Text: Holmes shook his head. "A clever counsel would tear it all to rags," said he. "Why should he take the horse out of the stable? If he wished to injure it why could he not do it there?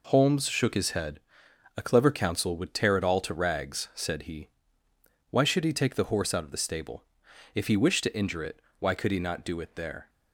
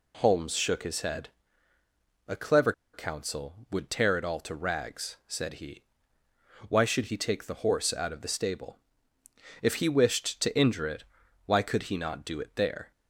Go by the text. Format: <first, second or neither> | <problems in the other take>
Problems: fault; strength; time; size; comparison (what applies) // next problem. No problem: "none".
first | pauses between "clever" and "counsel"; slight; at 2.7 s; 0.21 s long // pauses between "it" and "why"; at 11.0 s; 0.40 s long; slight in the first